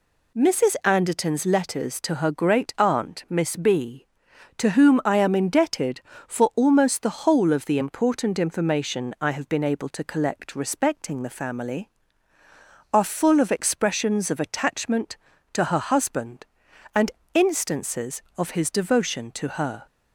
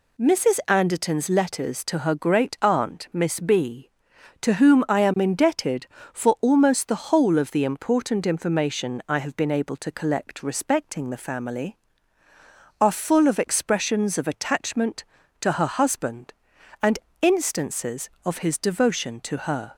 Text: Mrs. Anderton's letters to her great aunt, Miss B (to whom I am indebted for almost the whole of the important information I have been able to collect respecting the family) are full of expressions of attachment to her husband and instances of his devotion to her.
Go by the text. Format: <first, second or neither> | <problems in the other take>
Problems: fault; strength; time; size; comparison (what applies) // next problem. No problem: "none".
neither | pauses between "and" and "instances"; slight; the same in both